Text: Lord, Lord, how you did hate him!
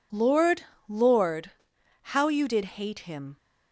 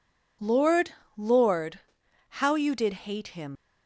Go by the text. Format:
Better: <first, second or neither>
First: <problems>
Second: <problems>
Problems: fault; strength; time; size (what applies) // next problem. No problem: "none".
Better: first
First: pauses between "did" and "hate"; slight; at 2.6 s; 0.16 s long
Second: pauses between "did" and "hate"; slight; at 2.9 s; 0.16 s long // leaves "him" unfinished; at 3.5 s; 95 ms